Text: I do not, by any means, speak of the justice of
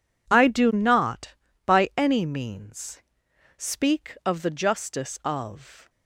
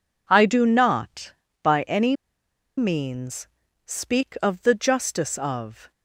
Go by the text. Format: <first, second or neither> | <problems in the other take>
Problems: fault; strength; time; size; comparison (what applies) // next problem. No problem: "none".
first | pauses between "any" and "means"; noticeable; at 2.1 s; 0.63 s long